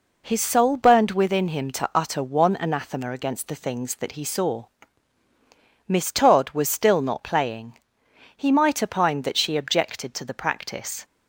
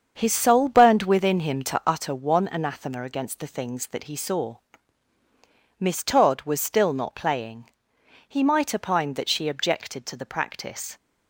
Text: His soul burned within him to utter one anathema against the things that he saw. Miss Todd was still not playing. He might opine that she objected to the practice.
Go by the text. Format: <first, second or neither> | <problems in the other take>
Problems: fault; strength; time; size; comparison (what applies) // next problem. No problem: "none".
first | starts louder than the rest; strong; until 2.1 s; 7 dB